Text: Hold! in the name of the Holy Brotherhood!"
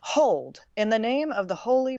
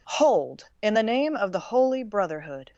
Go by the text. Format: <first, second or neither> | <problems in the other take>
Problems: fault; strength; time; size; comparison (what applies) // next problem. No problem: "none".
second | stops before "Brotherhood"; at 1.9 s